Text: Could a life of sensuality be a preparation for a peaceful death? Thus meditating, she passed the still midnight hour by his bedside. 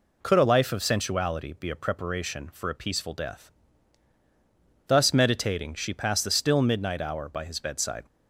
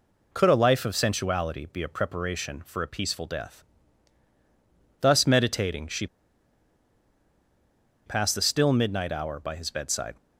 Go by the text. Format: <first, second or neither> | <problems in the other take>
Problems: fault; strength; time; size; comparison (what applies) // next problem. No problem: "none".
first | pauses between "she" and "passed"; strong; at 6.0 s; 2.0 s long